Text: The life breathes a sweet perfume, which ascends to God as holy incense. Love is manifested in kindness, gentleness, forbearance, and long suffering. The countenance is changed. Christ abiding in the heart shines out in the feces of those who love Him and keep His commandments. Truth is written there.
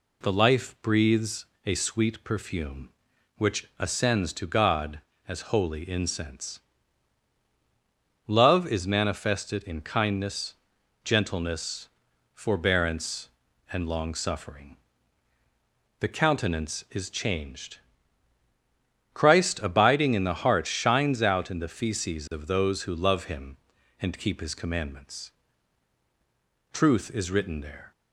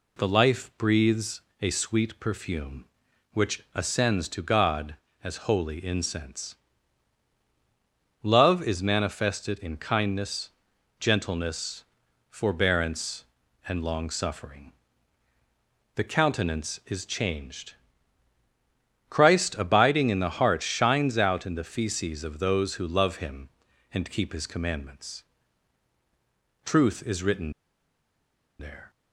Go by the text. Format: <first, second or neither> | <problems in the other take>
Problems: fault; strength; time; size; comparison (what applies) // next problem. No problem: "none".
first | pauses between "breathes" and "a"; slight; at 1.4 s; 0.20 s long; slight in the first // pauses between "written" and "there"; at 27.5 s; 1.0 s long